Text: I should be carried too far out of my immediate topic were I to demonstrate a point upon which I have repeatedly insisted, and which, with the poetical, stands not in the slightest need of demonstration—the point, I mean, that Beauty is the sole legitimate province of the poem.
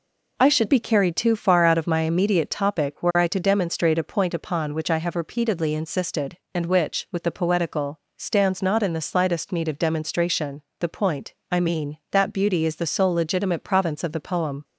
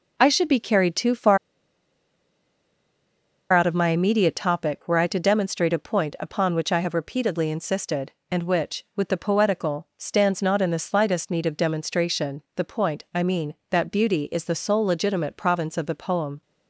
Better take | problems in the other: first | pauses between "far" and "out"; strong; at 1.3 s; 2.1 s long

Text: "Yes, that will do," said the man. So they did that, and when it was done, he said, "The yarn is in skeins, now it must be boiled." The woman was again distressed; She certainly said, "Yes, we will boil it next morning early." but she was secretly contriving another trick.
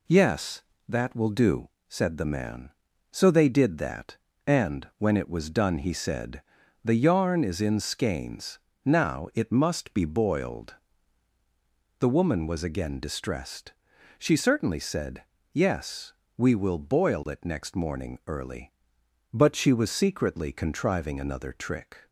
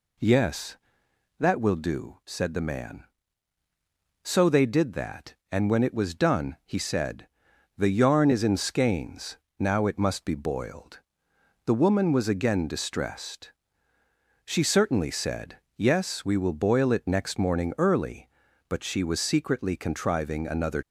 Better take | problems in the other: first | stops before "trick"; at 20.8 s

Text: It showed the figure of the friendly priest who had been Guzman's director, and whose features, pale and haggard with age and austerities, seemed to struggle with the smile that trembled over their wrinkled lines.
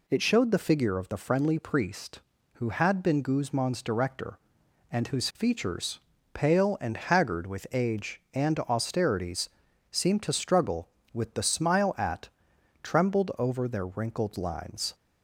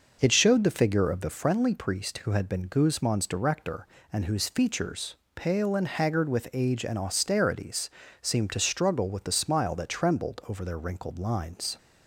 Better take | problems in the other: second | says "at" for "that"; at 11.9 s

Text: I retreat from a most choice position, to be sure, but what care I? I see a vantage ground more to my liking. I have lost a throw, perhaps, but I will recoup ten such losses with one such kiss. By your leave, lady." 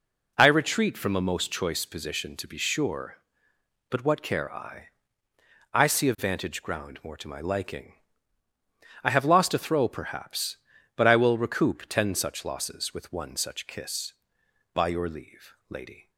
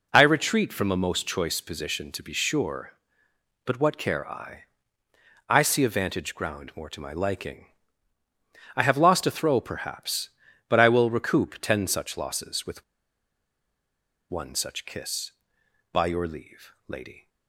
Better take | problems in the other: first | pauses between "with" and "one"; strong; at 12.8 s; 1.4 s long

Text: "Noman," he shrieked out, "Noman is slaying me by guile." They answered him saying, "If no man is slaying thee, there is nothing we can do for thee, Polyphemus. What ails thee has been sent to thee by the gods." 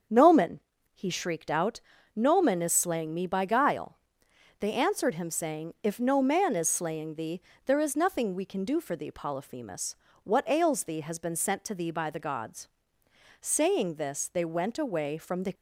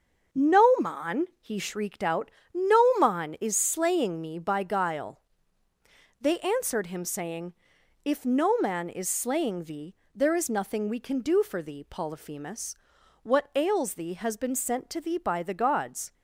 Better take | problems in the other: second | starts louder than the rest; strong; until 1.4 s; 7 dB; also in the second // goes on to say "Saying this they went away from the"; strong; from 13.3 s on; 2.1 s long

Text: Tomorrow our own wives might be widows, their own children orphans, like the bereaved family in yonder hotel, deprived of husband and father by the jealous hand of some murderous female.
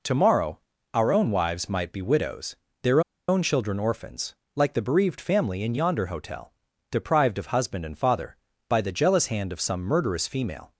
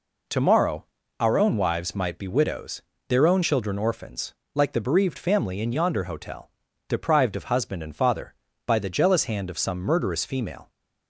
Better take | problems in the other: second | pauses between "Tomorrow" and "our"; slight; at 0.5 s; 0.36 s long; slight in the second // pauses between "their" and "own"; slight; at 3.0 s; 0.28 s long

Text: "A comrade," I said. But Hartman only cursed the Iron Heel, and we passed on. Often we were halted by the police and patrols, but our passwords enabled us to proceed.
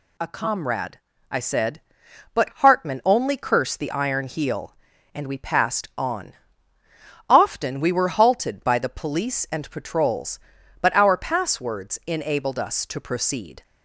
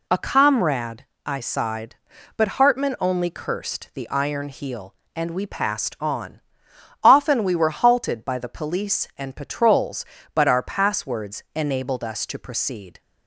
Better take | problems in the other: first | says "sighed" for "said"; at 1.4 s

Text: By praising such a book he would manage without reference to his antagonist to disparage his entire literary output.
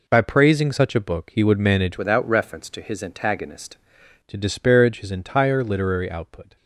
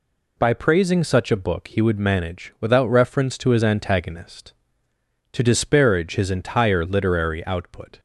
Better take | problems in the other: second | changes voice from "without" to "antagonist"; from 1.9 to 3.7 s; 1.8 s long

